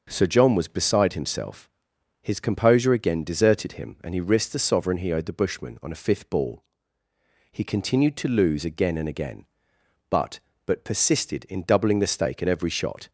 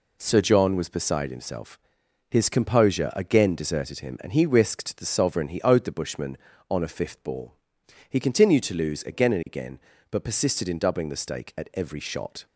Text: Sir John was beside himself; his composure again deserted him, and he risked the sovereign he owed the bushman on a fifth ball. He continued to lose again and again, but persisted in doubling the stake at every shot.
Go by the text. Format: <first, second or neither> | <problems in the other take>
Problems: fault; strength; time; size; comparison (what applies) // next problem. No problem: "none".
second | starts louder than the rest; noticeable; until 1.1 s; 6 dB // says "but" twice; at 10.6 s